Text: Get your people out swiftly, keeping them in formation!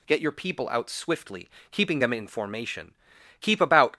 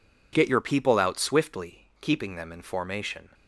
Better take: second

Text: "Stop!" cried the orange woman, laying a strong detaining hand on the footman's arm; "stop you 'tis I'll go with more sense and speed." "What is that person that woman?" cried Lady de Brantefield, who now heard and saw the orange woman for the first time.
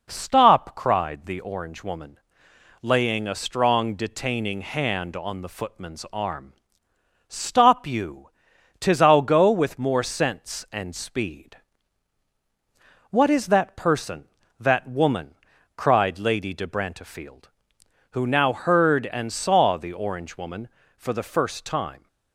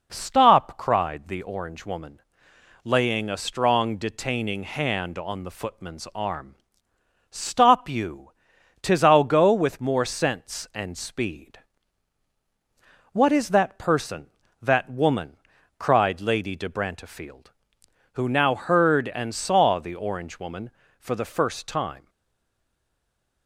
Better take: first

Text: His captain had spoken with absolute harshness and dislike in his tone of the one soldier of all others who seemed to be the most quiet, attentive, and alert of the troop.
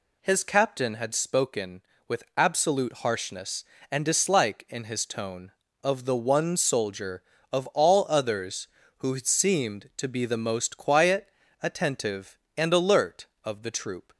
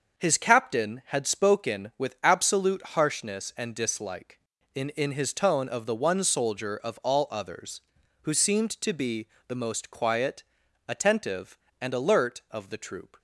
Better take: first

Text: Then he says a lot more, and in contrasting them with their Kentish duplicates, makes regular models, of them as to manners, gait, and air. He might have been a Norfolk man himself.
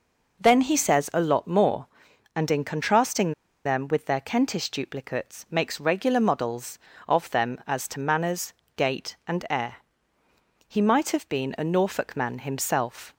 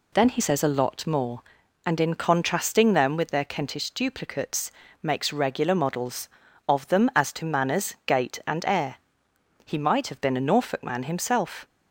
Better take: second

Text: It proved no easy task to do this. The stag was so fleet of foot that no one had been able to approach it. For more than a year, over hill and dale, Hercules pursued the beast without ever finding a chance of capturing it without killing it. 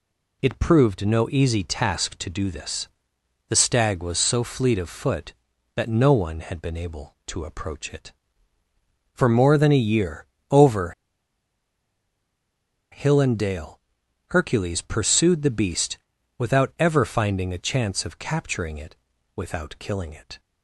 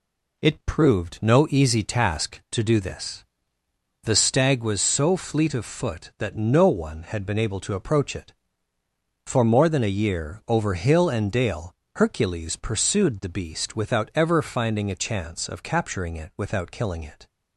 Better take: second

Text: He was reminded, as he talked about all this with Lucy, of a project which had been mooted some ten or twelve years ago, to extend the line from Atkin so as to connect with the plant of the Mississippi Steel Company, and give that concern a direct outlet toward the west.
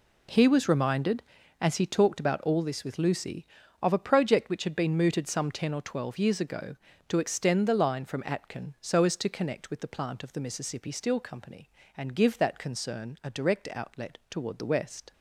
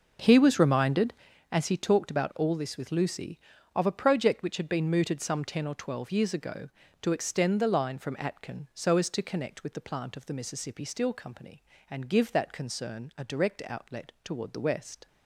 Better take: first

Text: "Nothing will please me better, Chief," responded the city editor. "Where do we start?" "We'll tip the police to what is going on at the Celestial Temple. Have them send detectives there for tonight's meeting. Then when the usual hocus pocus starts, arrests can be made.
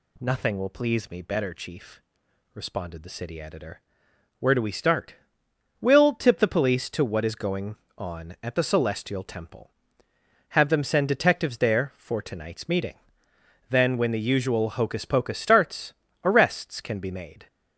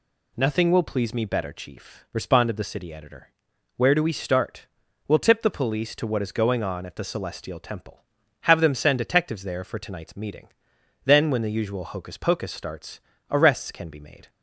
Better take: neither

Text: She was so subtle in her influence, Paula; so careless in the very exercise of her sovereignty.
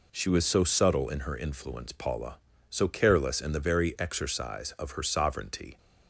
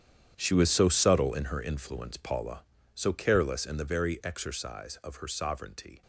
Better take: first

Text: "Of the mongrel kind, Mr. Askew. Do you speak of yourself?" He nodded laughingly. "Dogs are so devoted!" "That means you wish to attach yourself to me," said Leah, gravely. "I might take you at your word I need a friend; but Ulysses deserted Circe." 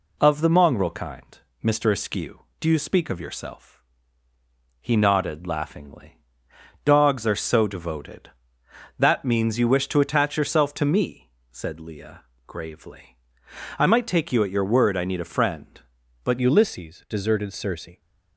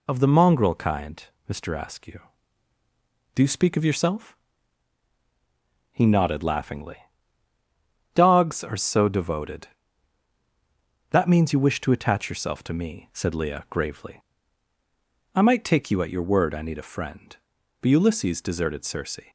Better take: second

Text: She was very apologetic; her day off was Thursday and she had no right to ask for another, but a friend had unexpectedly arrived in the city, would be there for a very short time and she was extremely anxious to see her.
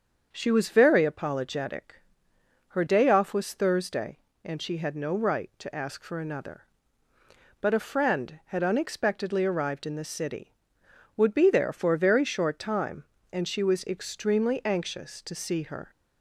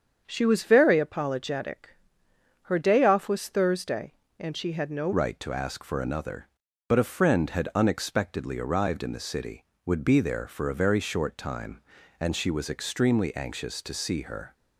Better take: first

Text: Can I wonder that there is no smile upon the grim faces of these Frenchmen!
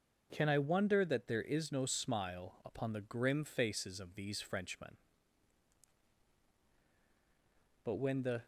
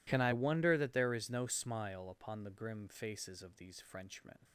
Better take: second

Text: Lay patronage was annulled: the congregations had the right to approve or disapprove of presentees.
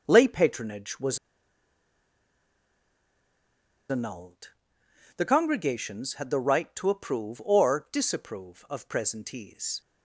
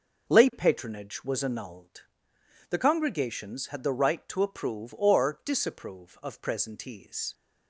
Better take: second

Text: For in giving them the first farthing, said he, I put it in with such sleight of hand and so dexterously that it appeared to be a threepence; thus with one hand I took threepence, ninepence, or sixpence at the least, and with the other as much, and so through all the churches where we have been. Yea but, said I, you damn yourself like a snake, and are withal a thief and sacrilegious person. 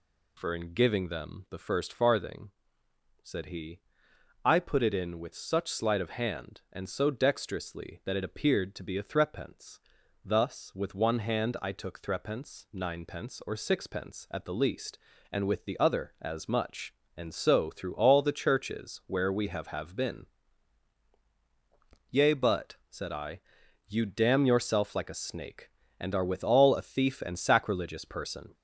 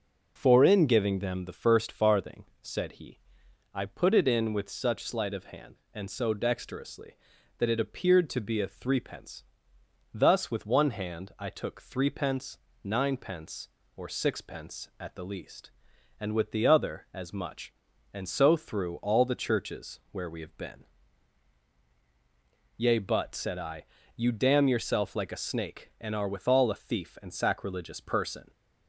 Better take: second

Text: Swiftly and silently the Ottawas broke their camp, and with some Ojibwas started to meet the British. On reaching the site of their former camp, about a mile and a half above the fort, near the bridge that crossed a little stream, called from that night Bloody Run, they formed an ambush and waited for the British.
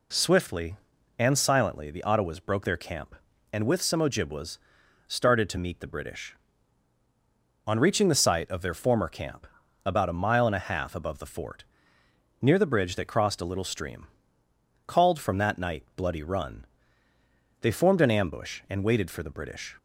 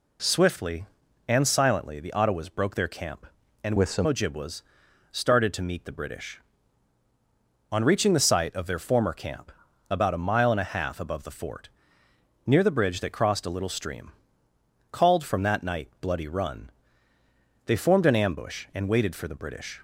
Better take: first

